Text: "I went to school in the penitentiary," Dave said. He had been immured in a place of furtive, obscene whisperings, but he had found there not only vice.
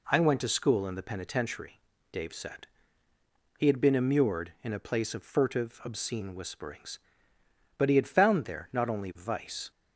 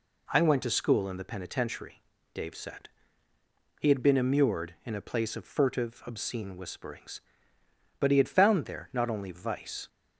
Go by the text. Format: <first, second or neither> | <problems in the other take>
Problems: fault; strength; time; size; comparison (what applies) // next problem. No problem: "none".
neither | none